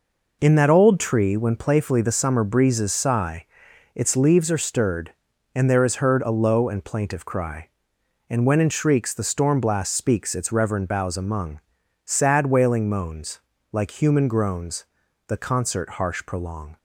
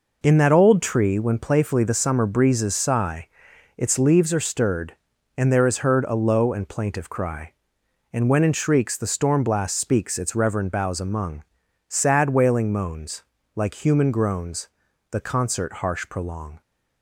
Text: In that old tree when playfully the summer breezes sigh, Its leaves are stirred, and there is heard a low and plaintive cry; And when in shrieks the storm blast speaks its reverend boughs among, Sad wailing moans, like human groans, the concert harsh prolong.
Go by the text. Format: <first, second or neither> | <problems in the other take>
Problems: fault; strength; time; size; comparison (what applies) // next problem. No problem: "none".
neither | none